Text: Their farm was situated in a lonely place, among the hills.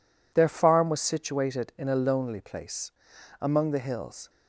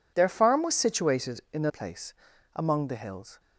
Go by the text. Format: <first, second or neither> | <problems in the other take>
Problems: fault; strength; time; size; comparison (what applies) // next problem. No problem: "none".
first | skips "lonely"; at 1.6 s